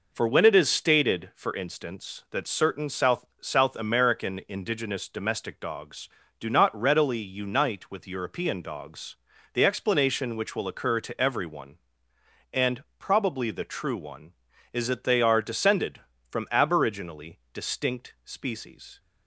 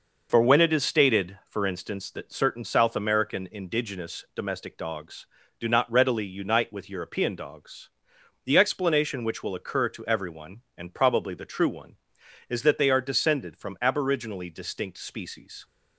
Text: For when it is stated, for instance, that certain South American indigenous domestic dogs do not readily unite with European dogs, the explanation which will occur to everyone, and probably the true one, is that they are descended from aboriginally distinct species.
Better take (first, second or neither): second